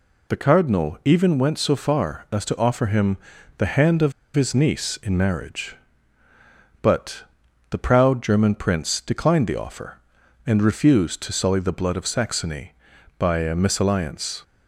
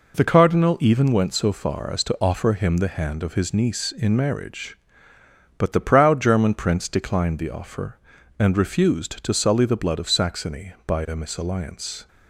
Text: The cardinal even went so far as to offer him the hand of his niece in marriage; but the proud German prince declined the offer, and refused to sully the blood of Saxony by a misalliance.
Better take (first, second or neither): second